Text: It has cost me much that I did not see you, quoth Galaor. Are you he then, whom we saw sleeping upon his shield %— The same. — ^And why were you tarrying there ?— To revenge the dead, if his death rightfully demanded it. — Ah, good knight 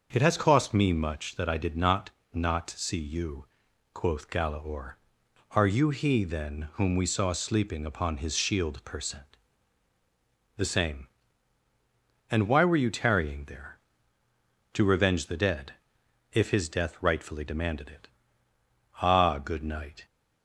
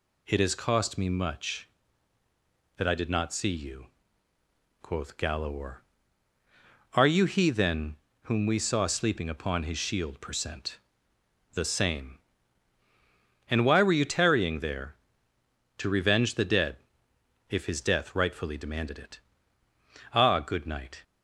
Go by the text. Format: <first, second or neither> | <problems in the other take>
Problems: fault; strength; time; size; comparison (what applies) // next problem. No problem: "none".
second | starts louder than the rest; until 1.1 s; 6.5 dB // says "not" twice; at 2.3 s